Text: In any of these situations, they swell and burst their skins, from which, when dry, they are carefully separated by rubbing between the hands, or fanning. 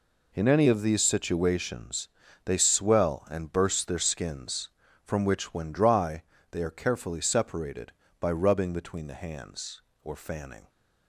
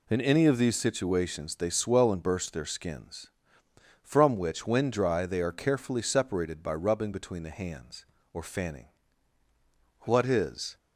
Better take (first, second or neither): first